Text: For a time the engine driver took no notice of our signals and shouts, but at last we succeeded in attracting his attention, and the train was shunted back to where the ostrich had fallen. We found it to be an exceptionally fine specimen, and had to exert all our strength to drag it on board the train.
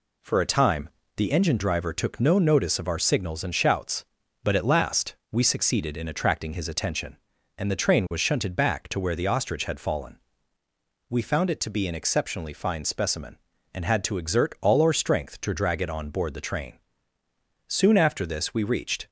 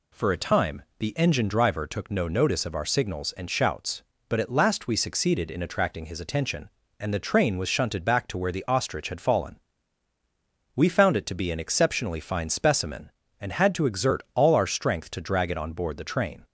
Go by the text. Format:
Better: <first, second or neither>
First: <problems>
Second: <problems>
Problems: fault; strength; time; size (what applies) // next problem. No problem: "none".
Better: second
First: pauses between "time" and "the"; slight; at 0.8 s; 0.28 s long // pauses between "last" and "we"; slight; at 5.1 s; 0.16 s long // goes on to say "Soon after this we reached"; from 17.6 s on; 1.4 s long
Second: pauses between "time" and "the"; slight; at 0.8 s; 0.16 s long